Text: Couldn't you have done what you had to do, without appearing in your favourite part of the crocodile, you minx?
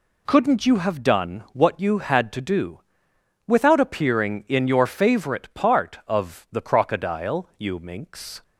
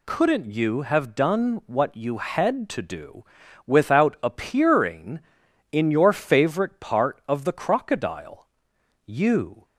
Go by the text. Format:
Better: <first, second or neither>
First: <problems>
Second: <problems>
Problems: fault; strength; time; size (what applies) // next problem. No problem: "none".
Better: first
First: none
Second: stops before "minx"; at 9.6 s